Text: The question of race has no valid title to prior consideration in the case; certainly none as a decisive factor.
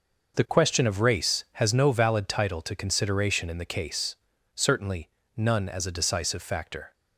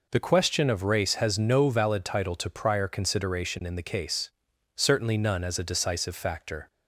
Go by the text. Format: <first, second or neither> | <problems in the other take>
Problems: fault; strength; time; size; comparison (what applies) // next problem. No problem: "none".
second | skips "prior"; at 2.7 s // pauses between "certainly" and "none"; slight; at 5.0 s; 0.28 s long